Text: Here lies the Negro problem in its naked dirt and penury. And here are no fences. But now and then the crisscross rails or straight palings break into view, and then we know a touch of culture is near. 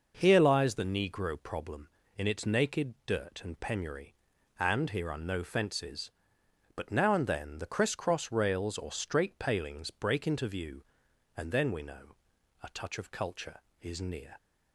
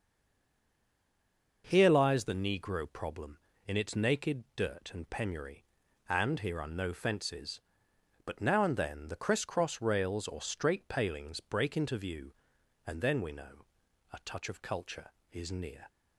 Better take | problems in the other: first | stays silent before the first word; noticeable; until 1.6 s; 1.6 s long // pauses between "know" and "a"; noticeable; at 13.6 s; 0.48 s long; noticeable in the first

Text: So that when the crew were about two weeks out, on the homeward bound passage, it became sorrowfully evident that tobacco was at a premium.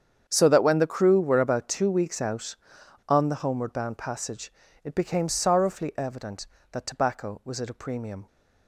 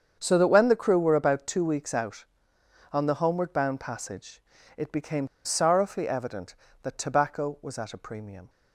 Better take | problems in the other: first | starts louder than the rest; strong; until 1.2 s; 7 dB; strong in the first // pauses between "became" and "sorrowfully"; slight; at 5.2 s; 0.17 s long

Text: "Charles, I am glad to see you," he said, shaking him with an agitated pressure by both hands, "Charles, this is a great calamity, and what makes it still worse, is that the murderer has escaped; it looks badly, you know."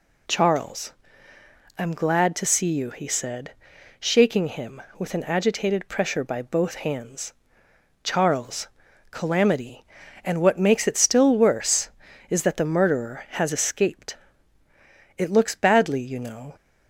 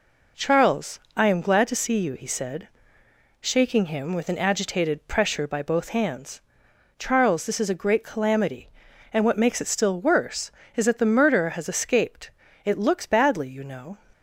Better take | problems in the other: second | skips "this is a great"; at 8.8 s

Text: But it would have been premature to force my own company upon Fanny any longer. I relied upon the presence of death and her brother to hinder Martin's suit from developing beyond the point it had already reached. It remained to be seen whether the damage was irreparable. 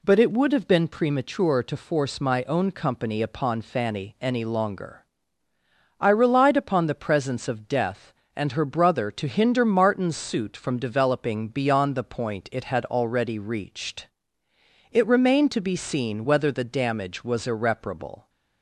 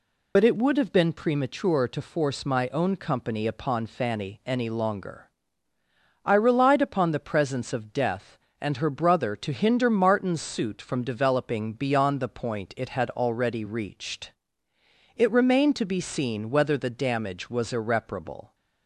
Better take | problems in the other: first | loses the start of "But"; at 0.3 s; 70 ms

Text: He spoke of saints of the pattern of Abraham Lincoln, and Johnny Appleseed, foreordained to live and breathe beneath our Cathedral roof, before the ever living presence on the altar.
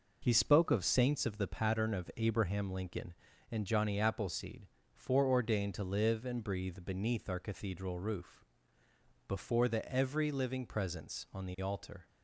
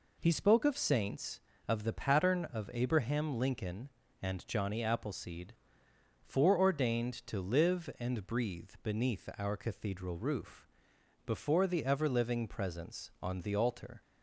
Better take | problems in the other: second | says "every" for "ever"; at 9.9 s

